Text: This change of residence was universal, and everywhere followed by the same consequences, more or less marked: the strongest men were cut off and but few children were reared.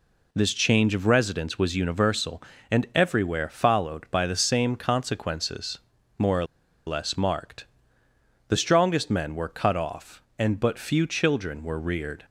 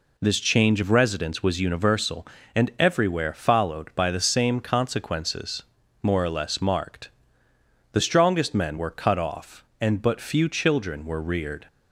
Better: second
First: pauses between "or" and "less"; at 6.4 s; 0.42 s long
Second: none

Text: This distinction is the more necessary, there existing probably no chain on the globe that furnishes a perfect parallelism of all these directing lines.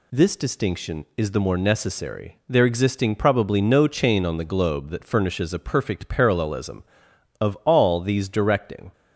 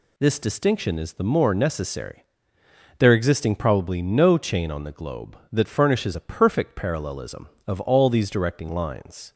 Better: second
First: stops before "lines"; at 8.9 s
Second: none

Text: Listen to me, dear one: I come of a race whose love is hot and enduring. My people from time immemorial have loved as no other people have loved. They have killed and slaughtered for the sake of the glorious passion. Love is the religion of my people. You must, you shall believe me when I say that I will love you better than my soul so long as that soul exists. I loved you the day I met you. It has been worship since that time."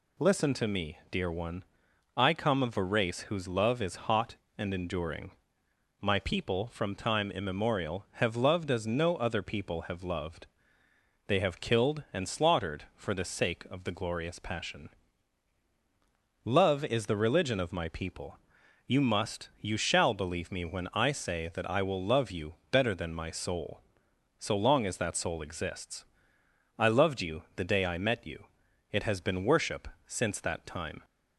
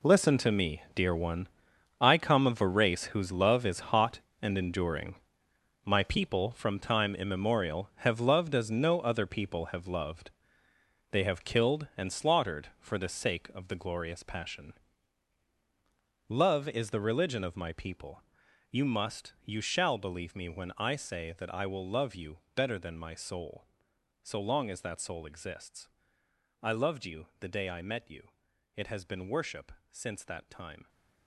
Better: first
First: pauses between "you" and "better"; slight; at 22.5 s; 0.18 s long // pauses between "worship" and "since"; slight; at 29.8 s; 0.18 s long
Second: gets quieter; strong; throughout; 13 dB // pauses between "you" and "better"; slight; at 22.3 s; 0.18 s long // pauses between "worship" and "since"; slight; at 29.7 s; 0.18 s long

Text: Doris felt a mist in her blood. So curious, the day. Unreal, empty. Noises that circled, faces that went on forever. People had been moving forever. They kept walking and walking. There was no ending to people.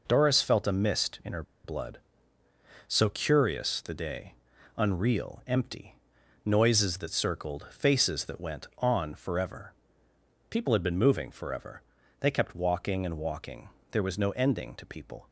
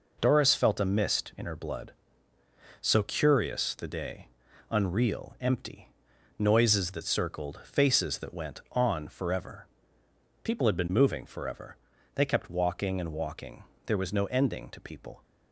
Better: second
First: pauses between "her" and "blood"; slight; at 1.4 s; 0.21 s long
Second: none

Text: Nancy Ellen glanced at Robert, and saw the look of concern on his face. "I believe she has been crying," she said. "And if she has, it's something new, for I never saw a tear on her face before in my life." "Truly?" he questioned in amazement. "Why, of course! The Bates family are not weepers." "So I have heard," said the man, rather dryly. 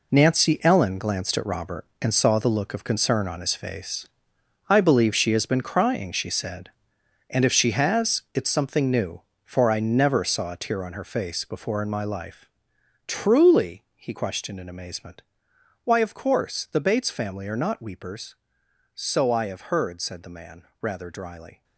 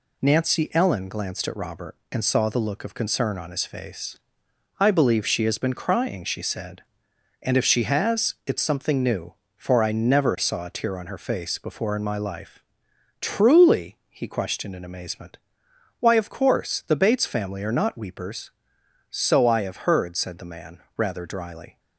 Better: second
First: gets quieter; strong; throughout; 10.5 dB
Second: none

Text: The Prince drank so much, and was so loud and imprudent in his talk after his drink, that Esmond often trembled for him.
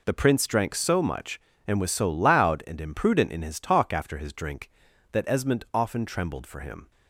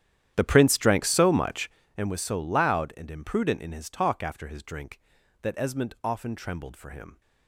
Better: first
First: none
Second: starts louder than the rest; strong; until 2.0 s; 10.5 dB

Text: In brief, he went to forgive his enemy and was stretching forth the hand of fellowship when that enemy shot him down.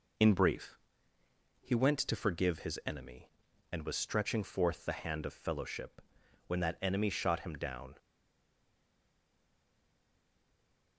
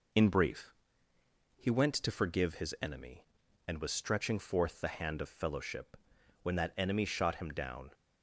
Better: second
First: pauses between "fellowship" and "when"; noticeable; at 5.9 s; 0.48 s long // stays silent after the last word; strong; from 7.9 s on; 3.0 s long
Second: pauses between "fellowship" and "when"; noticeable; at 5.9 s; 0.48 s long

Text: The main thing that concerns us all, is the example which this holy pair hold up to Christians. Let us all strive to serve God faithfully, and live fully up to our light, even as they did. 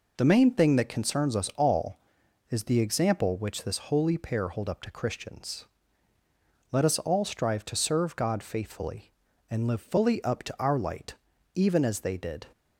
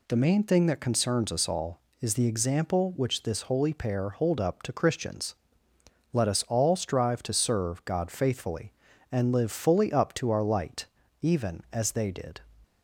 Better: neither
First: none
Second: none

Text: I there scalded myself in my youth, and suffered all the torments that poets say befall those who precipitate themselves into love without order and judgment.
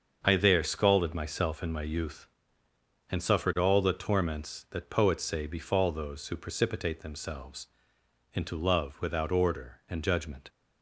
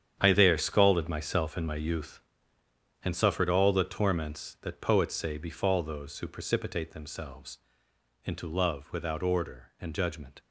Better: first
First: starts louder than the rest; until 1.2 s; 6.5 dB // pauses between "themselves" and "into"; noticeable; at 7.6 s; 0.66 s long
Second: gets quieter; strong; throughout; 12 dB // starts louder than the rest; strong; until 1.2 s; 9 dB // pauses between "themselves" and "into"; noticeable; at 7.5 s; 0.66 s long

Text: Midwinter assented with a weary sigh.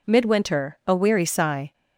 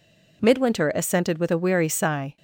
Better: second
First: skips "assented with"; at 0.8 s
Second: none

